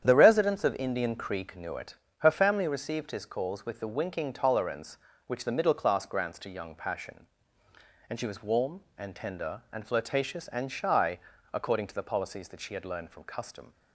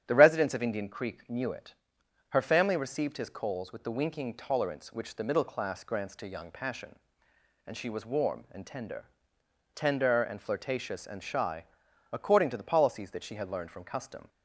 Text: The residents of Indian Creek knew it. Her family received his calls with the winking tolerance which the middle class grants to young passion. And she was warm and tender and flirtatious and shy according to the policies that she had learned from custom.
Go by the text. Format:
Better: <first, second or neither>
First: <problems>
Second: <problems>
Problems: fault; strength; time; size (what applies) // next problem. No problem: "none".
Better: first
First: starts louder than the rest; strong; until 1.0 s; 9 dB // pauses between "shy" and "according"; slight; at 11.1 s; 0.34 s long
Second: starts louder than the rest; strong; until 1.0 s; 10 dB // says "tender" twice; at 9.7 s // pauses between "shy" and "according"; noticeable; at 11.6 s; 0.48 s long